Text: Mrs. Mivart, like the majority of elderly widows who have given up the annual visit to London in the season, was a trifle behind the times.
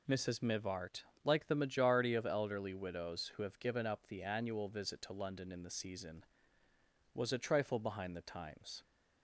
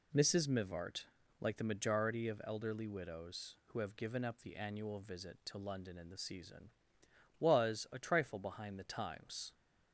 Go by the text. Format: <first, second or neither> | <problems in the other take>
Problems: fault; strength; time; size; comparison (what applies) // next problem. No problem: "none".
neither | none